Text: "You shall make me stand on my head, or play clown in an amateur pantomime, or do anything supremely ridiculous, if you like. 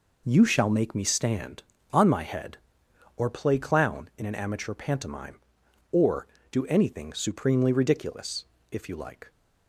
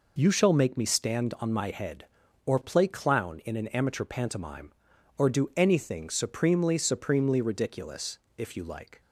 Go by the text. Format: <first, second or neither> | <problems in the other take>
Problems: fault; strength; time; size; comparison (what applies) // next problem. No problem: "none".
first | says "supremely" twice; at 6.7 s